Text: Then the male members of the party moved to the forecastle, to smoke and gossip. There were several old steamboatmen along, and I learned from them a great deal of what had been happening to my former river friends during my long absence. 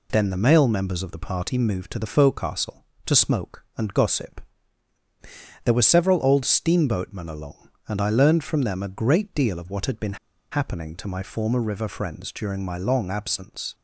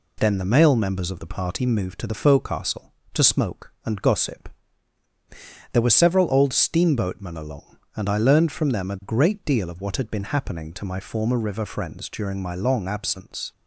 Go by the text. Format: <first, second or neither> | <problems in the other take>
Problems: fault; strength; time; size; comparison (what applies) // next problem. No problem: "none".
second | pauses between "been" and "happening"; at 10.1 s; 0.36 s long